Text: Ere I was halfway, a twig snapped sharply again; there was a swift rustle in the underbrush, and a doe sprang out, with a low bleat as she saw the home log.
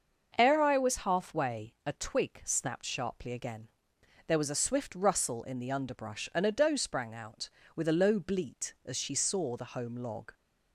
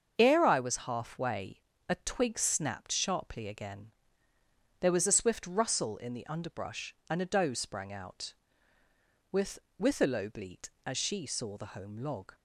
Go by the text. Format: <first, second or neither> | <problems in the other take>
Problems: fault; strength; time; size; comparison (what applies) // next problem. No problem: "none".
first | starts louder than the rest; until 1.1 s; 7 dB; noticeable in the first // says "with" twice; at 9.7 s